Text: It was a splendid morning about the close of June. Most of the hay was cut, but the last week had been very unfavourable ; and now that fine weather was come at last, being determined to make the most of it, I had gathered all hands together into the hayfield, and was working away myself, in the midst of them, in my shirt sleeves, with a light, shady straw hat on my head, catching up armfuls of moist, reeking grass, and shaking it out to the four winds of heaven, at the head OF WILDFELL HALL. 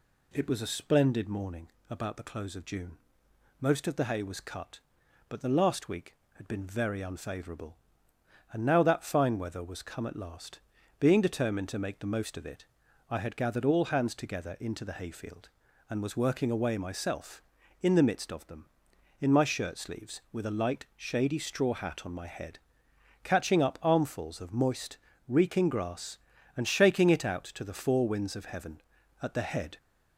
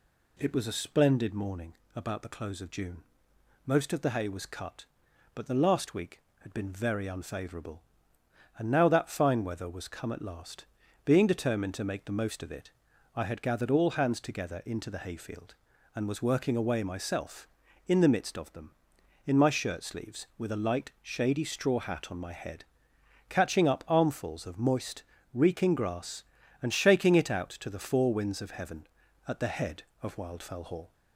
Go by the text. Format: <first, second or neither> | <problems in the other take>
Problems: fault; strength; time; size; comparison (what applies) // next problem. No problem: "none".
second | pauses between "morning" and "about"; slight; at 1.7 s; 0.18 s long; slight in the second // stops before "OF WILDFELL HALL"; at 29.7 s